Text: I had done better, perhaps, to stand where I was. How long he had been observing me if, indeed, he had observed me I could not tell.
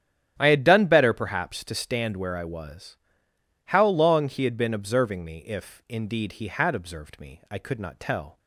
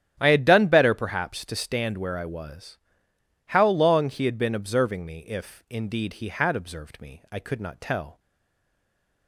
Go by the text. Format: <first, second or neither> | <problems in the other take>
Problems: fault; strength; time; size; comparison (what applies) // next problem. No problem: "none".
first | starts louder than the rest; strong; until 1.2 s; 11 dB; strong in the first // stays silent after the last word; from 8.1 s on; 1.1 s long